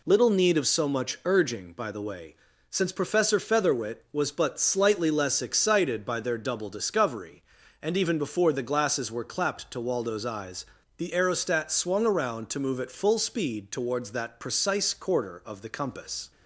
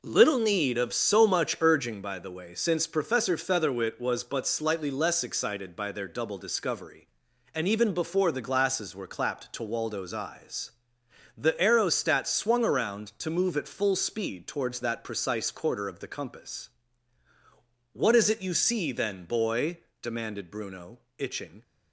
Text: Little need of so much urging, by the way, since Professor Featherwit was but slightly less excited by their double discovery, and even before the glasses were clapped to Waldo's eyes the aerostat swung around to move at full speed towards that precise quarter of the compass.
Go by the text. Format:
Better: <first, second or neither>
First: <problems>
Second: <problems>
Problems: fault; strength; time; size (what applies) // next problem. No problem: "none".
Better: first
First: pauses between "eyes" and "the"; slight; at 10.6 s; 0.32 s long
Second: pauses between "eyes" and "the"; noticeable; at 10.7 s; 0.70 s long // goes on to say "What is it you see then boy demanded Bruno itching"; strong; from 17.9 s on; 3.7 s long